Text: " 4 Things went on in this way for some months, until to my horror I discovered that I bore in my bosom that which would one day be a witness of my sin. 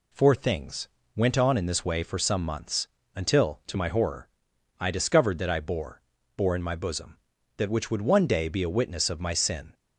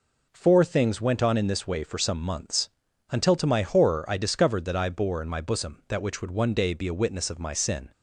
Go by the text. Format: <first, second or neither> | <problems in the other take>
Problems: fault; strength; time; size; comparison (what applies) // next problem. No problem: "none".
second | pauses between "Things" and "went"; slight; at 0.8 s; 0.26 s long // pauses between "horror" and "I"; noticeable; at 4.2 s; 0.50 s long // says "bore" twice; at 6.3 s